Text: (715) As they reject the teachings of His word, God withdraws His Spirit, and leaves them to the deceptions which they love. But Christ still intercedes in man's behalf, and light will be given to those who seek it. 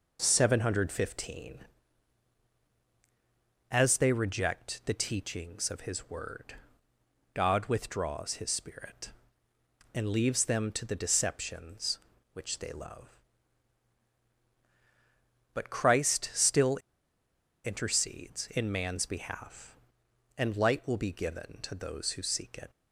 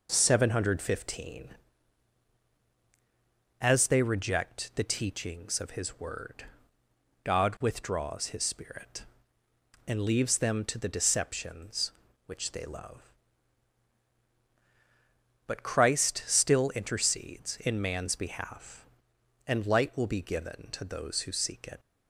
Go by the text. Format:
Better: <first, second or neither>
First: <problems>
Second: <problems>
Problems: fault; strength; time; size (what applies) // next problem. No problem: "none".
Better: second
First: pauses between "still" and "intercedes"; noticeable; at 16.7 s; 0.89 s long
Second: none